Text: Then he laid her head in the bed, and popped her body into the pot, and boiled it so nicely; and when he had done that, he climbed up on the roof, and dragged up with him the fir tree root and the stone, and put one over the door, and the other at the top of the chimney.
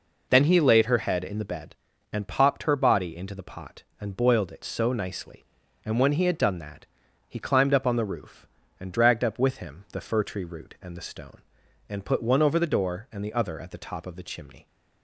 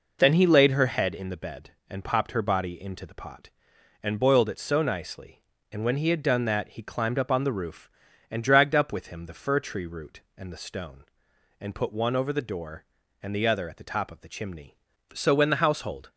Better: first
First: none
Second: goes on to say "So when the household"; noticeable; from 15.1 s on; 0.98 s long

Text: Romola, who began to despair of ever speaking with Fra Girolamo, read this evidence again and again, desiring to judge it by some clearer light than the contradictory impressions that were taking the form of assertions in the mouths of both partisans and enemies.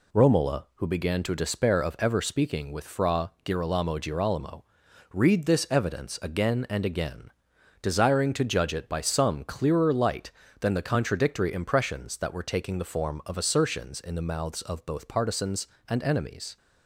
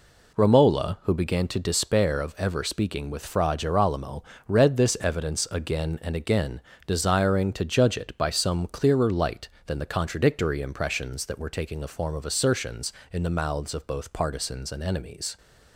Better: second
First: says "Girolamo" twice; at 3.9 s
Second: none

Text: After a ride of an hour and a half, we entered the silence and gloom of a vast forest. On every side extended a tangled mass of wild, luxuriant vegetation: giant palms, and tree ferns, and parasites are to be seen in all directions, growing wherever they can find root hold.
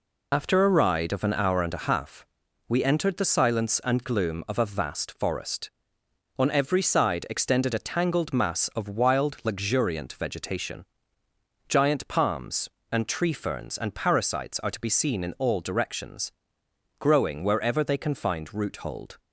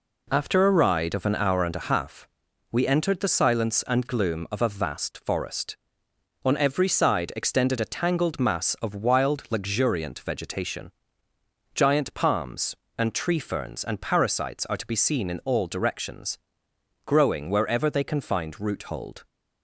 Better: second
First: loses the start of "After"; at 0.3 s; 65 ms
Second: none

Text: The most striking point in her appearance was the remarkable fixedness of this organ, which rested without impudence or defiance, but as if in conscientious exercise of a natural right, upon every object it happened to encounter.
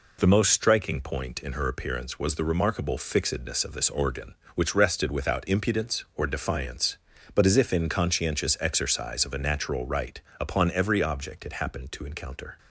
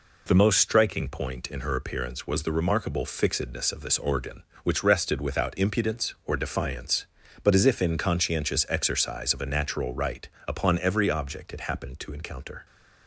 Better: neither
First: none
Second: none

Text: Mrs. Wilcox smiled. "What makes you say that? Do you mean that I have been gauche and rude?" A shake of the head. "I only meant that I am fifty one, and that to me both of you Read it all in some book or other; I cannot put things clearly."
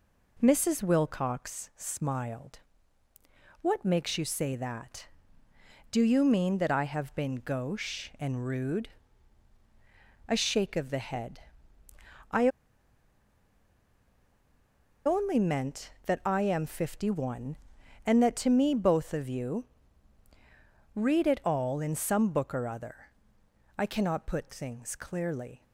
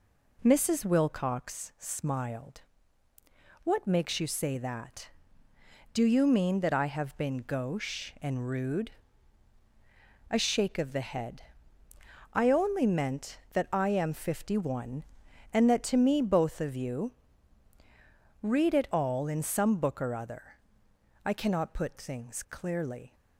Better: second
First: pauses between "I" and "only"; strong; at 12.4 s; 2.5 s long // pauses between "you" and "Read"; strong; at 19.6 s; 1.3 s long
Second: pauses between "you" and "Read"; strong; at 17.1 s; 1.3 s long

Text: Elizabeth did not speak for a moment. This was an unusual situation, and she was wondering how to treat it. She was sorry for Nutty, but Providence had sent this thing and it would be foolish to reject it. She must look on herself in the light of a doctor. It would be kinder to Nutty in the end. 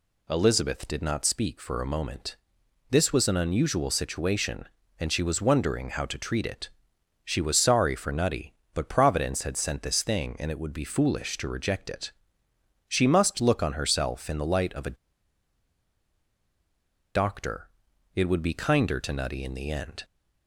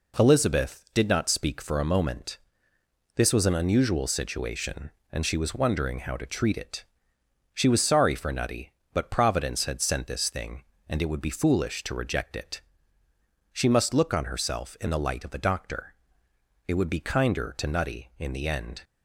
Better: second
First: pauses between "a" and "doctor"; strong; at 14.9 s; 2.1 s long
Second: none

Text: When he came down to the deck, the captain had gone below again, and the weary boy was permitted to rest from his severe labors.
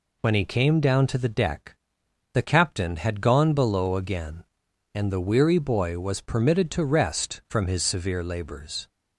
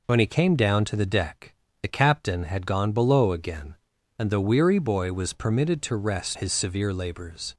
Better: first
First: none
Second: skips "from"; at 6.3 s

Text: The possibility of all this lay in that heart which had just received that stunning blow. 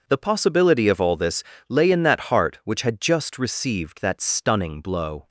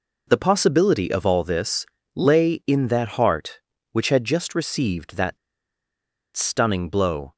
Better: first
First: pauses between "this" and "lay"; slight; at 1.4 s; 0.26 s long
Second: pauses between "this" and "lay"; slight; at 1.8 s; 0.28 s long // pauses between "that" and "stunning"; at 5.3 s; 0.99 s long

